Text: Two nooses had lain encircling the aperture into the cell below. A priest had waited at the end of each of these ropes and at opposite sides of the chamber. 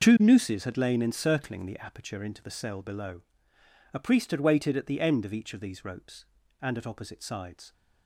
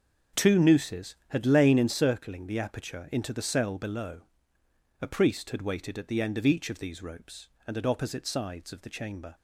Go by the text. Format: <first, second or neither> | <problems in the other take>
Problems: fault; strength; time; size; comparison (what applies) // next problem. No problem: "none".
second | starts louder than the rest; noticeable; until 1.0 s; 6 dB; also in the second // stops before "of the chamber"; at 7.7 s